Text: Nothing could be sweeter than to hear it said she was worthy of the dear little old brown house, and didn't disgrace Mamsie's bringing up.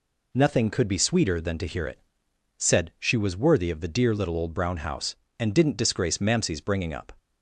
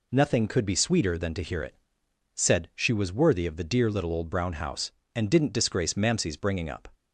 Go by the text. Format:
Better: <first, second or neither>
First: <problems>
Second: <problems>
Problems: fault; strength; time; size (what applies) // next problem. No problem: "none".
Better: neither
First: pauses between "it" and "said"; noticeable; at 1.9 s; 0.62 s long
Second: pauses between "it" and "said"; noticeable; at 1.7 s; 0.64 s long